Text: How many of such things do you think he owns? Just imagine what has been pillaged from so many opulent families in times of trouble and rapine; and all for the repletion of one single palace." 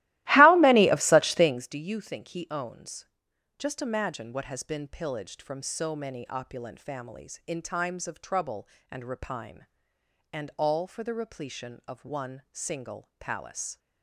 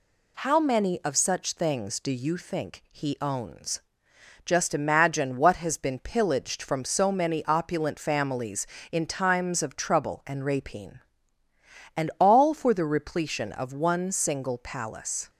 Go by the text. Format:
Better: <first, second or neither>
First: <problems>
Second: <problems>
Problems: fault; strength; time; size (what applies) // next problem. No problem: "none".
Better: second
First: starts louder than the rest; strong; until 1.7 s; 17 dB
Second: none